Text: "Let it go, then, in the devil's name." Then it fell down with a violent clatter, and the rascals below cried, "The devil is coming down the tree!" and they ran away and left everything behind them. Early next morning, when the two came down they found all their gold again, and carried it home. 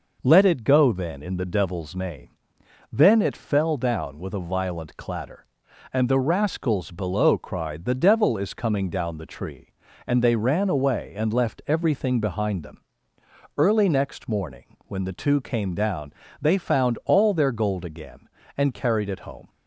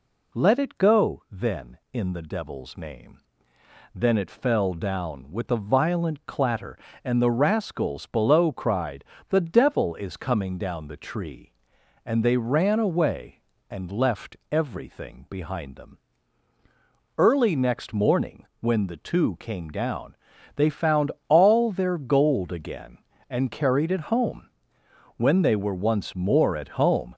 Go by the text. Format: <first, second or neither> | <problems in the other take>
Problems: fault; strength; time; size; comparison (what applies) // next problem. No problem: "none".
first | pauses between "down" and "they"; at 20.1 s; 0.42 s long; slight in the first // pauses between "found" and "all"; slight; at 21.1 s; 0.18 s long // goes on to say "When they were once more at home"; strong; from 25.1 s on; 1.9 s long